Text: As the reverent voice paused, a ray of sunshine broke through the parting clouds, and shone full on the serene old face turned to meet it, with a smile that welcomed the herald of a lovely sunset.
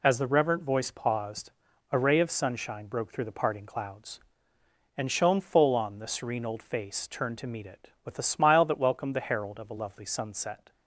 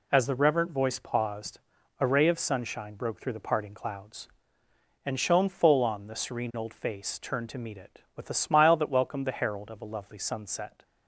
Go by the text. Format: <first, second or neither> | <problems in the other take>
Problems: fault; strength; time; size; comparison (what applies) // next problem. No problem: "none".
neither | none